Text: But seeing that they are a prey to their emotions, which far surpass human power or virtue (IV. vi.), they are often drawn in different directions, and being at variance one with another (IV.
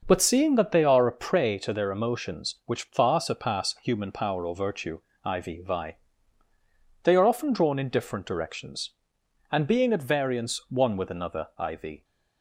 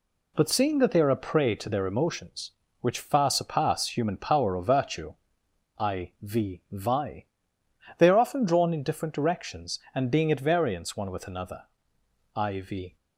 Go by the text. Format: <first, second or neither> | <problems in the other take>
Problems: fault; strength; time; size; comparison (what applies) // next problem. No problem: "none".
neither | none